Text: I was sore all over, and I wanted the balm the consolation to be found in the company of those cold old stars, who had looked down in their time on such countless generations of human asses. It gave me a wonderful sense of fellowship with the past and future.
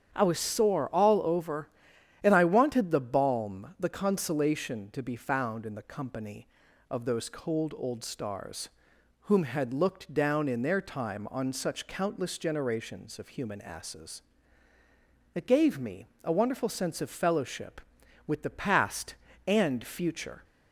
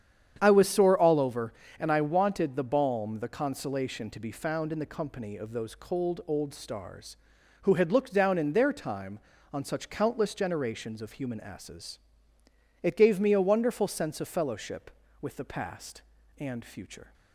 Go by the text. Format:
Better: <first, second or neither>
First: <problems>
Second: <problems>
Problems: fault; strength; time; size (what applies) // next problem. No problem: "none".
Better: second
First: starts louder than the rest; strong; until 1.1 s; 8.5 dB // says "whom" for "who"; at 9.2 s // pauses between "me" and "a"; slight; at 16.0 s; 0.16 s long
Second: starts louder than the rest; strong; until 1.4 s; 8.5 dB